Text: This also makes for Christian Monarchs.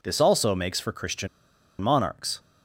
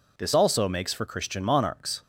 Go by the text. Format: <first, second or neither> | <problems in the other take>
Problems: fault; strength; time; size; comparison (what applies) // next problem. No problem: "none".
second | pauses between "Christian" and "Monarchs"; noticeable; at 1.2 s; 0.52 s long